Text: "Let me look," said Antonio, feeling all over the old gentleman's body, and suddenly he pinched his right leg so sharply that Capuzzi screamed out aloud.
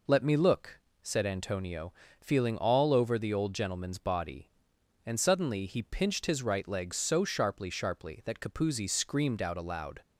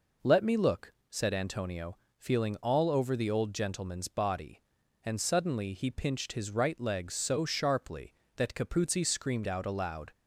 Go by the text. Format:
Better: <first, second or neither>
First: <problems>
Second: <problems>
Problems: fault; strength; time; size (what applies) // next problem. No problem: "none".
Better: second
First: says "sharply" twice; at 7.6 s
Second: none